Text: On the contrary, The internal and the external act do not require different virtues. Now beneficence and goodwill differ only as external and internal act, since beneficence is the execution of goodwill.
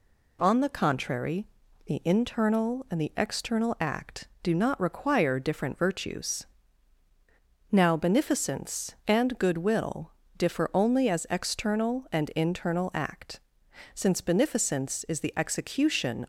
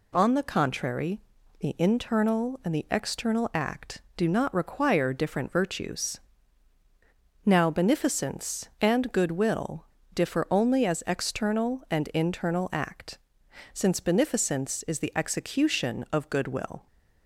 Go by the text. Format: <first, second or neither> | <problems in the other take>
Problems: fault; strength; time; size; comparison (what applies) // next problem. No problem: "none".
second | pauses between "goodwill" and "differ"; slight; at 10.1 s; 0.26 s long; slight in the second // stops before "of goodwill"; at 16.2 s